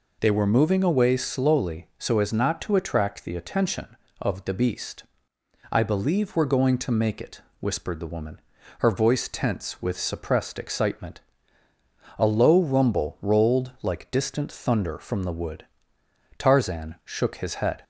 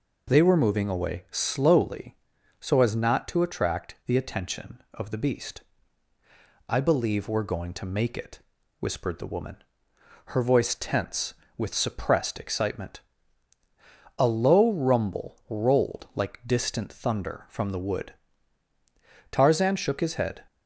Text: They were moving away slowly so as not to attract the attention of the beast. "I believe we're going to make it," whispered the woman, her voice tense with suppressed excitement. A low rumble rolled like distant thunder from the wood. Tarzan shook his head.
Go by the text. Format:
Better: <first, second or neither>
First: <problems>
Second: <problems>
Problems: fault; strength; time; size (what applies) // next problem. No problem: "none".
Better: neither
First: none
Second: none